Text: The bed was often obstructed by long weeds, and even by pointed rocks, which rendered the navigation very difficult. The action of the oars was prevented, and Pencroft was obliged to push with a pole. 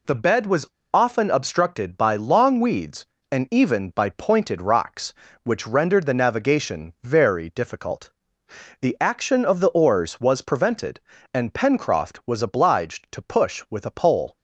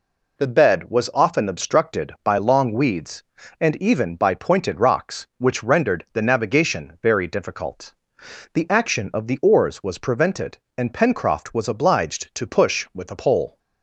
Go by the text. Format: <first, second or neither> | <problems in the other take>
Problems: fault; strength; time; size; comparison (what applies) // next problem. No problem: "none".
second | pauses between "was" and "often"; slight; at 0.6 s; 0.25 s long